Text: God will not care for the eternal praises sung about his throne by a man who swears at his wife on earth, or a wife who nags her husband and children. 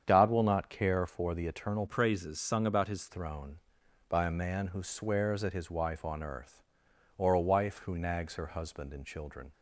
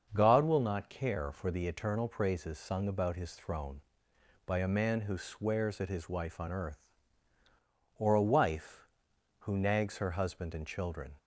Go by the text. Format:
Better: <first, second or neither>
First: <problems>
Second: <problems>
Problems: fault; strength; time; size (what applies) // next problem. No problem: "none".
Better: second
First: starts louder than the rest; strong; until 1.0 s; 8 dB // changes voice from "praises" to "his"; from 1.8 to 3.0 s; 1.2 s long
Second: starts louder than the rest; until 1.1 s; 6.5 dB